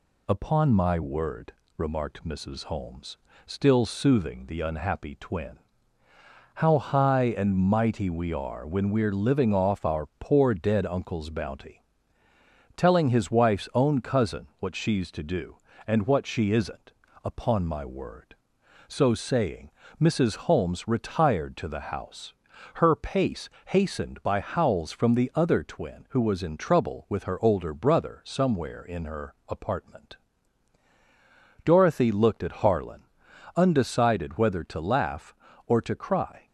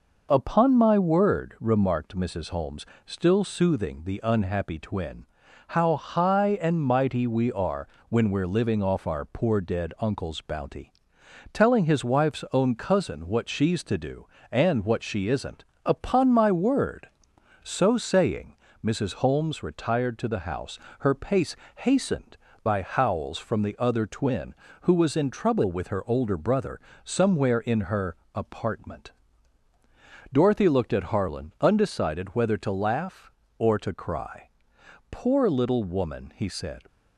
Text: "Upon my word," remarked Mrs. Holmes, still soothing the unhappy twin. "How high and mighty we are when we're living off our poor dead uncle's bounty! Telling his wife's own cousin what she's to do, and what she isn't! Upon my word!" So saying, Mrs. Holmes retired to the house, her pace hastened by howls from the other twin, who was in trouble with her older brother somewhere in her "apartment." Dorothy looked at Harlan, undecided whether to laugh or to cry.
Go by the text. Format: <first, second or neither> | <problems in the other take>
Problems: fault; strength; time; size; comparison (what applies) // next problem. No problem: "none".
first | pauses between "are" and "when"; slight; at 7.8 s; 0.22 s long // pauses between "pace" and "hastened"; slight; at 21.5 s; 0.22 s long; slight in the first // pauses between "brother" and "somewhere"; slight; at 26.7 s; 0.24 s long // pauses between "her" and "apartment"; slight; at 28.1 s; 0.22 s long; slight in the first // goes on to say "Poor little woman he said"; strong; from 35.0 s on; 1.7 s long